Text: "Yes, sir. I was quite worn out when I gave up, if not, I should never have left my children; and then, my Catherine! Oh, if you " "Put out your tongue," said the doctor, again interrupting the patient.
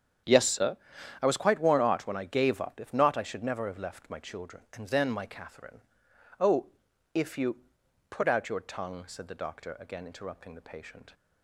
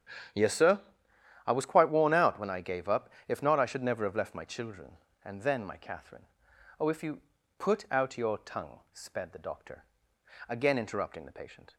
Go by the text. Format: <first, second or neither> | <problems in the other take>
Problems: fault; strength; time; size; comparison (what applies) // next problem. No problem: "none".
first | starts louder than the rest; strong; until 2.0 s; 9.5 dB; strong in the first // says "sped" for "said"; at 8.9 s